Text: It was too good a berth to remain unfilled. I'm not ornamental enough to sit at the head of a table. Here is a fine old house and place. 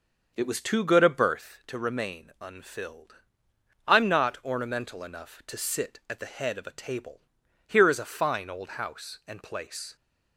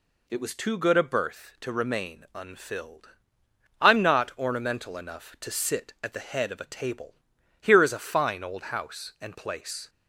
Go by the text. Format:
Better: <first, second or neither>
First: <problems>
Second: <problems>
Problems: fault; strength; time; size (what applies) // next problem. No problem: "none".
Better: second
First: starts louder than the rest; until 1.6 s; 6.5 dB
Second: none